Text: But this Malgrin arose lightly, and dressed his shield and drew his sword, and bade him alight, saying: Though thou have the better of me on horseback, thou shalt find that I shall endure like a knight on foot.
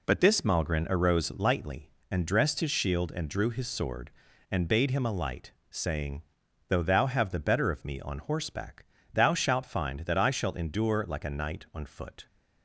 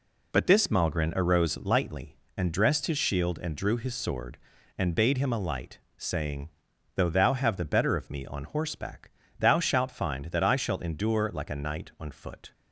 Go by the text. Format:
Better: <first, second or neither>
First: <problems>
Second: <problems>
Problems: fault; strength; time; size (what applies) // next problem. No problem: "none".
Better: neither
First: none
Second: none